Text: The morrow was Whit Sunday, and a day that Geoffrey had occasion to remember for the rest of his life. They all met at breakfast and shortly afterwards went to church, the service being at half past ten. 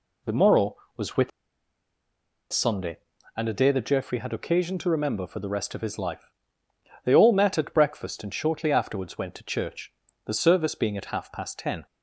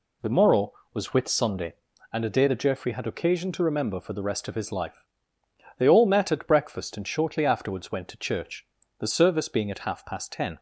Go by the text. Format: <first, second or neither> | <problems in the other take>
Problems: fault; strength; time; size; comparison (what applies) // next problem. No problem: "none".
second | pauses between "Whit" and "Sunday"; at 1.3 s; 1.2 s long